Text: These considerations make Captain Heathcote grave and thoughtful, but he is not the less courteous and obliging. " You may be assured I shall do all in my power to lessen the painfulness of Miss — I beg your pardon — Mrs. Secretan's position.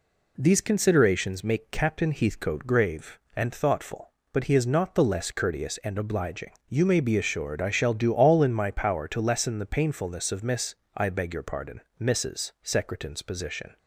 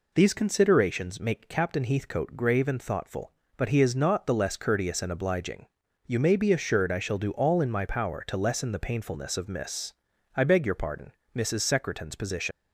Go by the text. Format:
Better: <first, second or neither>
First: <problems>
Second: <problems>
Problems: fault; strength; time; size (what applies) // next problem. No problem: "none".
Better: first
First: none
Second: leaves "position" unfinished; at 12.5 s; 125 ms